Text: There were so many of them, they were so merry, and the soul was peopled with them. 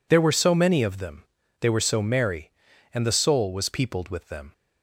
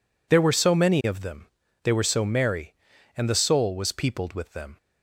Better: neither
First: none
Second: none

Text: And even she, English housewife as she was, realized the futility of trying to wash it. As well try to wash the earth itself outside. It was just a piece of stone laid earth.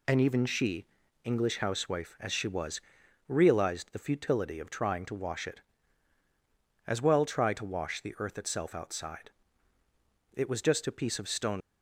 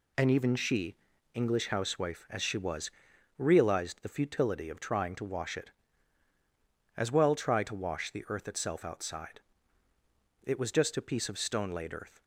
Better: second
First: stops before "laid earth"; at 11.6 s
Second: none

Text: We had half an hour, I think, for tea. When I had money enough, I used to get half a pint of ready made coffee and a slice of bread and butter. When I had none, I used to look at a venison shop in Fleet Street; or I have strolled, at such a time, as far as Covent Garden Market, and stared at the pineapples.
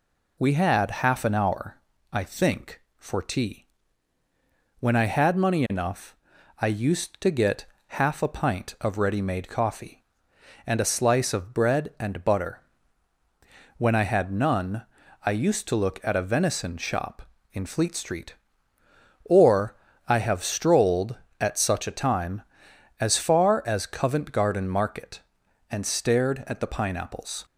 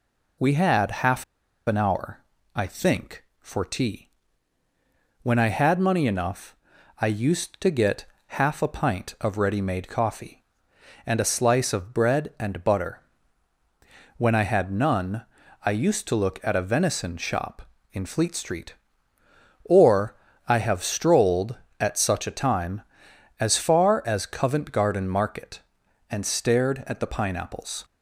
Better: first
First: pauses between "get" and "half"; slight; at 7.6 s; 0.22 s long // pauses between "or" and "I"; slight; at 19.7 s; 0.30 s long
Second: pauses between "half" and "an"; at 1.2 s; 0.42 s long // pauses between "get" and "half"; slight; at 8.0 s; 0.22 s long // pauses between "or" and "I"; slight; at 20.1 s; 0.30 s long

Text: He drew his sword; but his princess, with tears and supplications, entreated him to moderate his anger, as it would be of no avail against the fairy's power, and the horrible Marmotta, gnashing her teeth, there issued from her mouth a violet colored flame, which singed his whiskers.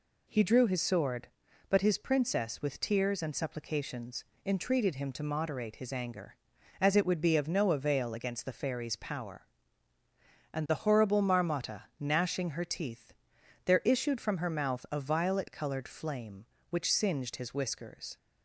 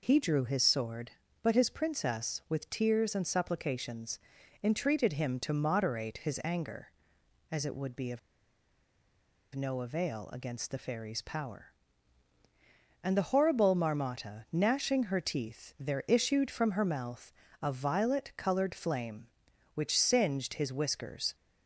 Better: first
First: none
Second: pauses between "of" and "no"; strong; at 8.1 s; 1.3 s long // pauses between "mouth" and "a"; slight; at 17.3 s; 0.30 s long

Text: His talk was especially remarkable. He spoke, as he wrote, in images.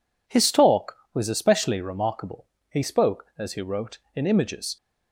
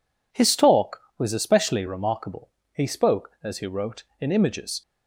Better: neither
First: none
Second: none

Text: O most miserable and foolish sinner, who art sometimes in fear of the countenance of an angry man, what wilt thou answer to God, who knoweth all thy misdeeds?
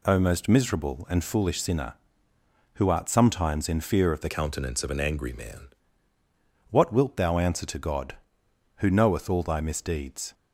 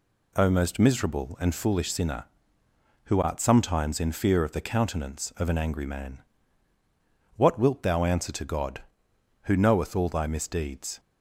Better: second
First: changes voice from "countenance" to "man"; from 4.2 to 5.6 s; 1.4 s long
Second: none

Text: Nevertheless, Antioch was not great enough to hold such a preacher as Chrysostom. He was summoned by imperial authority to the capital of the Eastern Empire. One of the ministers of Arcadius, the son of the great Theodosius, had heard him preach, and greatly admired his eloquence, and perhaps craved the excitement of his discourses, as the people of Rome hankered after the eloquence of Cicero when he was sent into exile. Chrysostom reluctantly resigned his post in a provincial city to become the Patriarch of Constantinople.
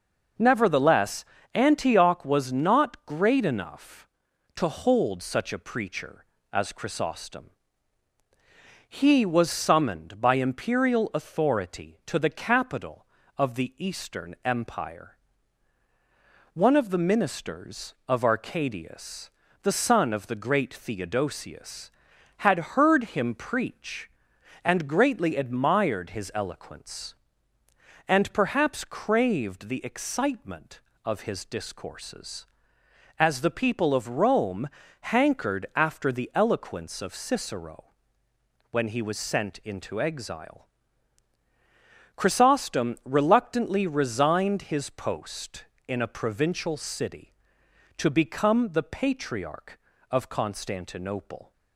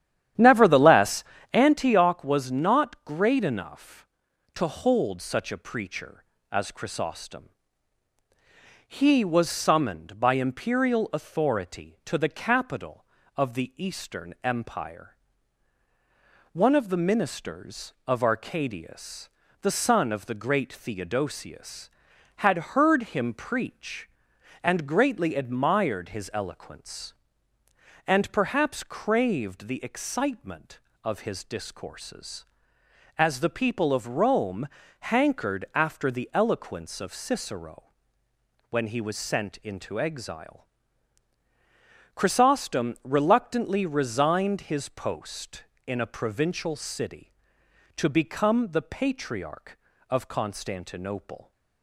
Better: first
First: pauses between "Rome" and "hankered"; slight; at 34.6 s; 0.32 s long // pauses between "Cicero" and "when"; noticeable; at 37.8 s; 0.84 s long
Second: starts louder than the rest; strong; until 1.7 s; 10.5 dB // pauses between "Rome" and "hankered"; slight; at 34.6 s; 0.32 s long // pauses between "Cicero" and "when"; noticeable; at 37.8 s; 0.84 s long

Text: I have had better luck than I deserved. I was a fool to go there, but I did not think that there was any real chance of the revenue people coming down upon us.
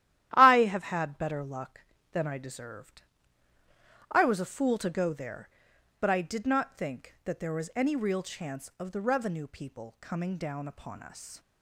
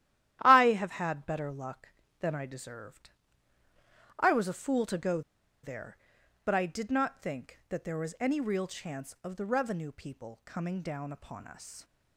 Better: first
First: starts louder than the rest; strong; until 1.3 s; 12.5 dB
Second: starts louder than the rest; strong; until 1.4 s; 12.5 dB // pauses between "go" and "there"; at 5.2 s; 0.43 s long

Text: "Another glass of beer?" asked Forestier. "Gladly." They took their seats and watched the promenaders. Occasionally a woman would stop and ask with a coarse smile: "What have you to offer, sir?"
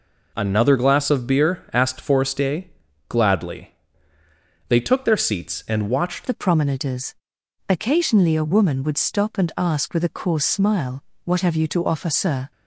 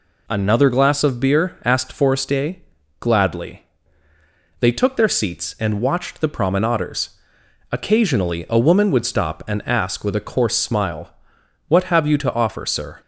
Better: second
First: changes voice at "the"; from 6.2 s on; 6.3 s long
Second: none

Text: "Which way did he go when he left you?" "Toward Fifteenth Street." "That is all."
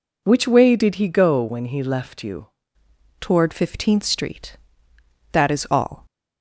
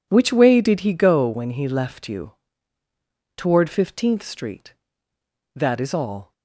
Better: second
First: changes voice at "Toward"; from 3.2 s on; 2.8 s long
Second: none

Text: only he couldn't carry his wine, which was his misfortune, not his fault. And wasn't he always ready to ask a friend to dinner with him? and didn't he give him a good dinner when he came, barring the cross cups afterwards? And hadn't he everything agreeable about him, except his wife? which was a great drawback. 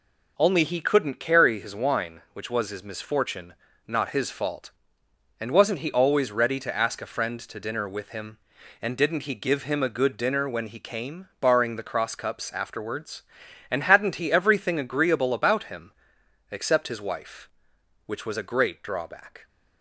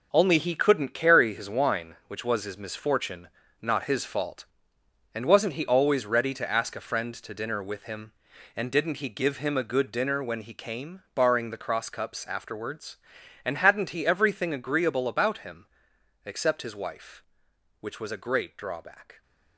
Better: first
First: none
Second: gets quieter; strong; throughout; 9 dB

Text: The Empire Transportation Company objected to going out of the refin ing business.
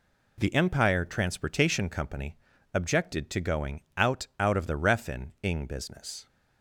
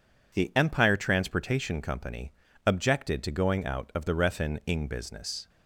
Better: second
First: pauses between "Company" and "objected"; slight; at 2.3 s; 0.36 s long // says "out" twice; at 4.3 s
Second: pauses between "Company" and "objected"; slight; at 2.3 s; 0.34 s long

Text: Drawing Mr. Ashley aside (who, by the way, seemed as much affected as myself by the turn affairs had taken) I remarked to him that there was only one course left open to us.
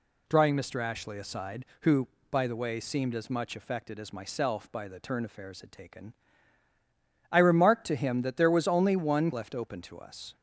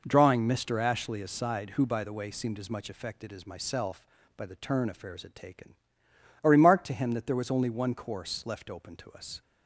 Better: second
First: skips "course"; at 9.3 s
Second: none

